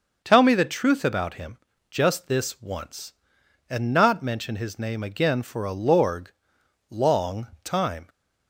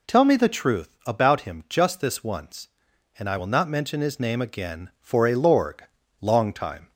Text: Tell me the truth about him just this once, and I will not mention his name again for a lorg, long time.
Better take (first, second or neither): second